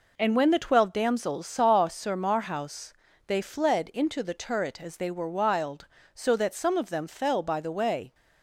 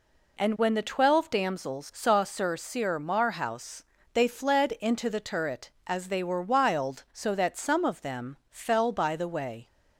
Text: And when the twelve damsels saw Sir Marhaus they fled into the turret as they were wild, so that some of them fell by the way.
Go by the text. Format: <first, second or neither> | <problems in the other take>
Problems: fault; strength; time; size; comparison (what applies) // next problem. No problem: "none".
first | says "Sir" twice; at 2.5 s // pauses between "Marhaus" and "they"; slight; at 3.8 s; 0.30 s long; slight in the first